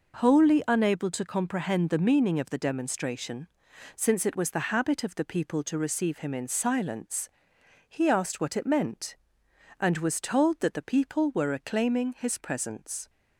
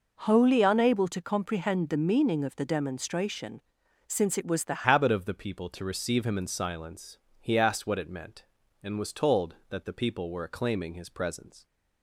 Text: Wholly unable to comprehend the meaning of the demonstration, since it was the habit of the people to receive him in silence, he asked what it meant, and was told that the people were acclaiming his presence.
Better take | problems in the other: first | changes voice at "habit"; from 4.8 s on; 6.8 s long

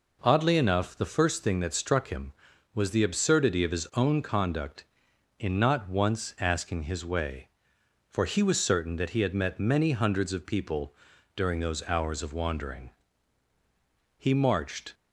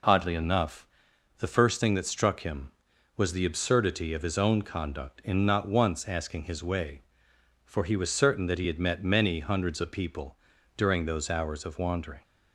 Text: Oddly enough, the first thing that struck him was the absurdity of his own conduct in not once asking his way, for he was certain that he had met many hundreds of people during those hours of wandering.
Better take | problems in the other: second | pauses between "people" and "during"; at 10.9 s; 0.40 s long; also in the second // goes on to say "He marched"; noticeable; from 14.1 s on; 0.78 s long

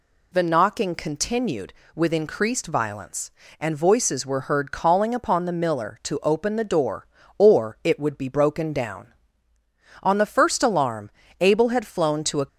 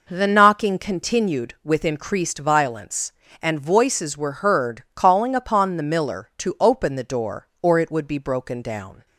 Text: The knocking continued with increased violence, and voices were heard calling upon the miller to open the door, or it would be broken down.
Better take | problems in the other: second | goes on to say "On the first alarm Abel had flown to a"; strong; from 10.0 s on; 2.4 s long

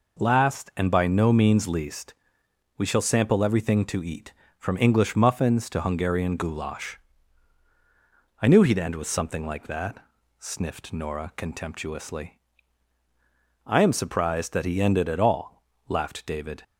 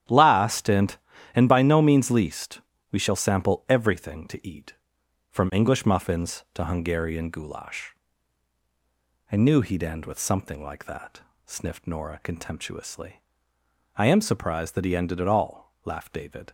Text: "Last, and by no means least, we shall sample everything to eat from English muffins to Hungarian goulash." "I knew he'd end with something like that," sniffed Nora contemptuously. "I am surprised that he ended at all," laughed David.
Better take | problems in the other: first | starts louder than the rest; strong; until 1.4 s; 10.5 dB // says "and" twice; at 1.3 s

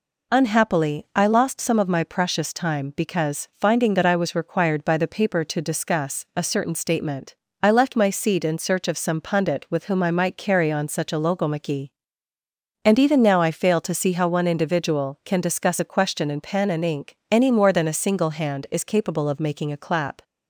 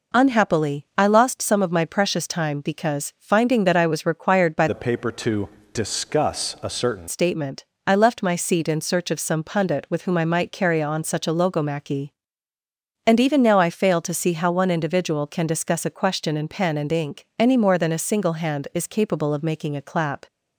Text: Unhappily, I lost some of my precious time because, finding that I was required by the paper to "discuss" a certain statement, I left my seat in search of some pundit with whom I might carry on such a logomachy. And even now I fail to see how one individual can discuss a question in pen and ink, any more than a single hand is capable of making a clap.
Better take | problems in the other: first | changes voice from "the" to "certain"; from 4.6 to 7.0 s; 2.4 s long // pauses between "to" and "discuss"; slight; at 5.4 s; 0.28 s long

